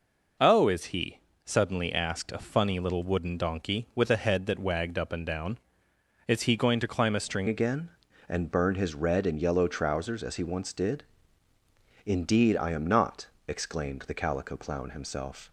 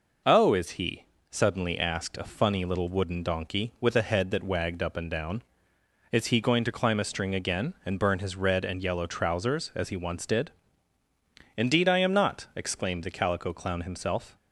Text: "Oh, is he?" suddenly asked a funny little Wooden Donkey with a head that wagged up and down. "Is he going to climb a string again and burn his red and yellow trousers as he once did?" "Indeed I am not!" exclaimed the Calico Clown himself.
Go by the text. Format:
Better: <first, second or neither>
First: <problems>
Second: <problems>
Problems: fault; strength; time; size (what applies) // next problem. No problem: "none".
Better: second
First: changes voice at "again"; from 7.4 s on; 8.1 s long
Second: none